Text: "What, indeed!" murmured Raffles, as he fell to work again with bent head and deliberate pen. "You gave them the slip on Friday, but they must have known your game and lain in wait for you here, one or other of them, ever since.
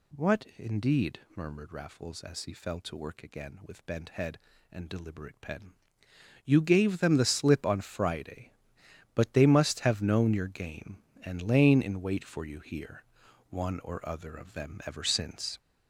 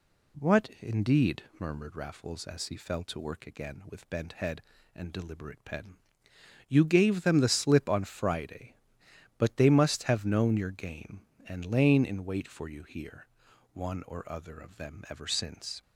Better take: second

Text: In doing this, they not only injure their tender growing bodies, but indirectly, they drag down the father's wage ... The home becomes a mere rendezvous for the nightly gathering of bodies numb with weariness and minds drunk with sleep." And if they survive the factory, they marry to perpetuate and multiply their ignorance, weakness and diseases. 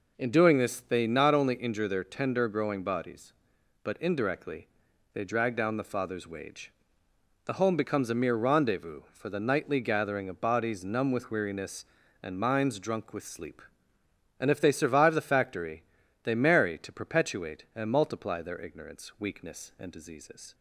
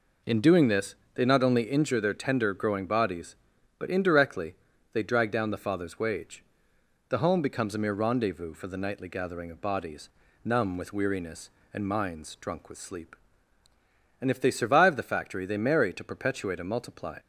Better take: first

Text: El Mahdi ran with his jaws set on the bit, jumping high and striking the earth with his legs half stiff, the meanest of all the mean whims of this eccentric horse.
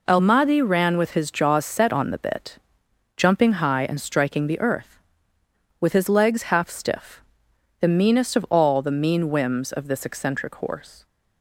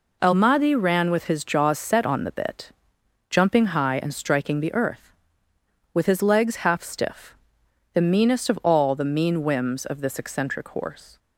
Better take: neither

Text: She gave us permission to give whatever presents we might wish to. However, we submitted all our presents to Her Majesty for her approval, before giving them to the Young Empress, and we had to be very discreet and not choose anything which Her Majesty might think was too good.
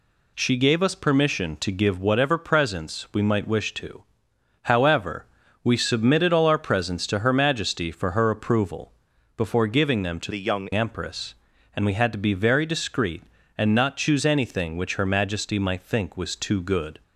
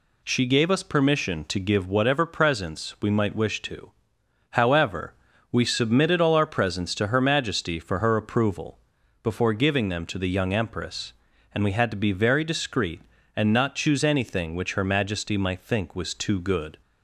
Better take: second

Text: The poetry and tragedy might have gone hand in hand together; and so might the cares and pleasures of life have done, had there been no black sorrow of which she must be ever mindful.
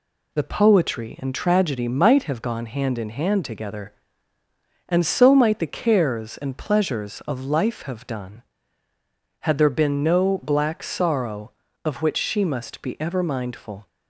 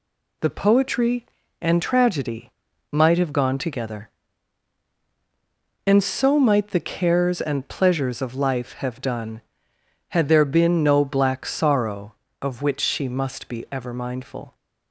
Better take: first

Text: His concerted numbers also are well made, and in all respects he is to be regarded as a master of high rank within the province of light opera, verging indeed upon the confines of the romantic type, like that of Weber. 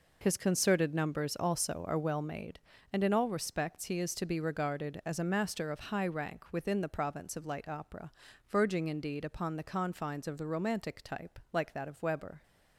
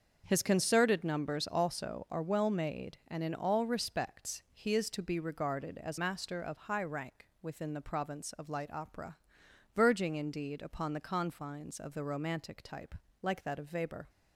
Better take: first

